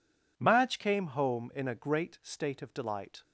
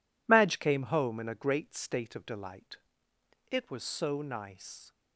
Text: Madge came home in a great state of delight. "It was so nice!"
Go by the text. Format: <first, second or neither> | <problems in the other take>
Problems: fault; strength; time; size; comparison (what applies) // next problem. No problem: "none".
second | stops before "It was so nice"; at 3.2 s